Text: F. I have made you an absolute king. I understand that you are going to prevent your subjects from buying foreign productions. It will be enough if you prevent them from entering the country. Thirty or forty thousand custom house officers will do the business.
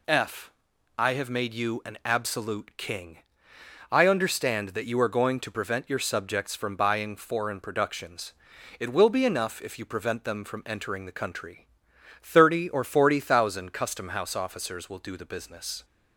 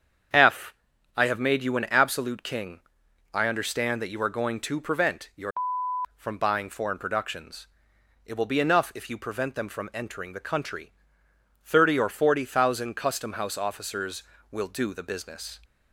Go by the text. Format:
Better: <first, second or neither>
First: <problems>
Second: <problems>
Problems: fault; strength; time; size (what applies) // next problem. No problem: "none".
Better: first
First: none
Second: starts louder than the rest; strong; until 1.7 s; 7.5 dB // skips "subjects"; at 5.8 s